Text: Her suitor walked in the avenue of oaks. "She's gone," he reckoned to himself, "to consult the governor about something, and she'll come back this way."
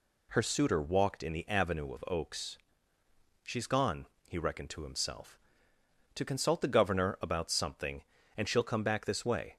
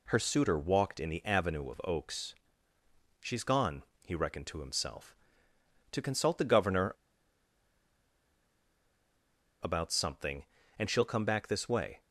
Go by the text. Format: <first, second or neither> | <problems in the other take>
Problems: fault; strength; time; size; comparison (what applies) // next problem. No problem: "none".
first | pauses between "governor" and "about"; strong; at 6.9 s; 2.6 s long